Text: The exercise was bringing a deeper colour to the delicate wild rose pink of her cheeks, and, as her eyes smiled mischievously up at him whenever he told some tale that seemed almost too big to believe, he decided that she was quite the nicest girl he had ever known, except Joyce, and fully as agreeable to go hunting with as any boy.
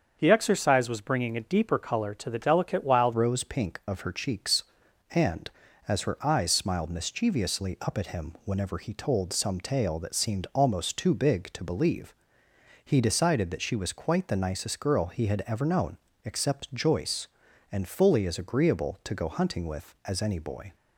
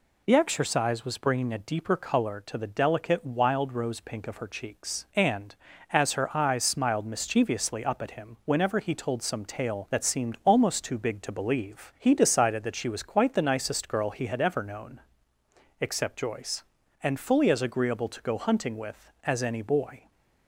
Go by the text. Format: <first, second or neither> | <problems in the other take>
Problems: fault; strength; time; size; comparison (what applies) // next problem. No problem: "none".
second | starts louder than the rest; until 1.2 s; 7 dB // changes voice at "rose"; from 3.1 s on; 17.6 s long